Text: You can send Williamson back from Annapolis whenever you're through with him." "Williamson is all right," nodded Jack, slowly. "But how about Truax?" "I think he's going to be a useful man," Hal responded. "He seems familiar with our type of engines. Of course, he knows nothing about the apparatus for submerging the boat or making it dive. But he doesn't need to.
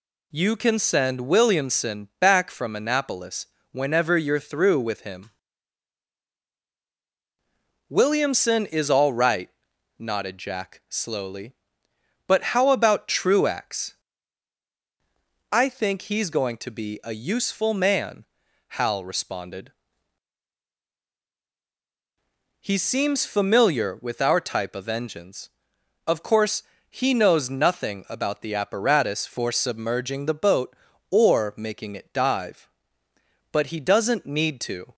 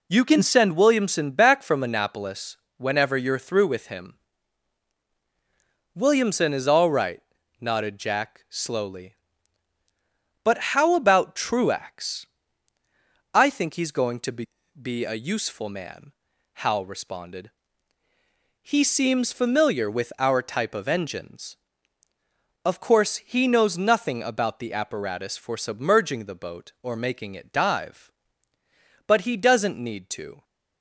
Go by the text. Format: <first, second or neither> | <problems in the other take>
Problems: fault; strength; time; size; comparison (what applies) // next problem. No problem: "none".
first | pauses between "Annapolis" and "whenever"; slight; at 2.5 s; 0.20 s long; slight in the first // pauses between "But" and "how"; slight; at 10.5 s; 0.16 s long // says "be" twice; at 14.7 s